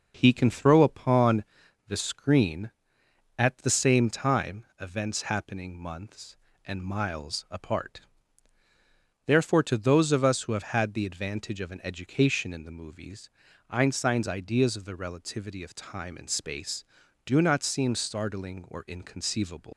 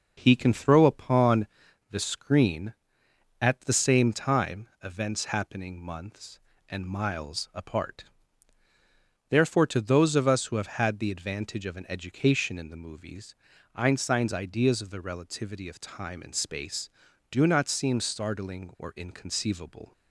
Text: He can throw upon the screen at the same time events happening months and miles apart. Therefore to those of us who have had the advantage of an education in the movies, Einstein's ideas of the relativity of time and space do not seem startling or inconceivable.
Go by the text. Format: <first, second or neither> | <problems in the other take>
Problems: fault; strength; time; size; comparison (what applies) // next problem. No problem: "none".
second | pauses between "upon" and "the"; at 1.4 s; 0.44 s long; also in the second // pauses between "time" and "events"; slight; at 4.6 s; 0.16 s long; slight in the second // leaves "inconceivable" unfinished; at 19.7 s; 100 ms